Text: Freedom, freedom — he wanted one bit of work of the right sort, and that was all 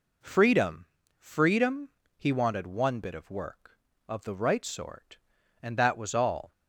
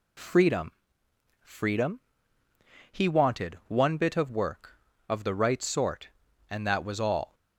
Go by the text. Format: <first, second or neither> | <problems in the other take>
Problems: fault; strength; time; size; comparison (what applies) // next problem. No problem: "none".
neither | none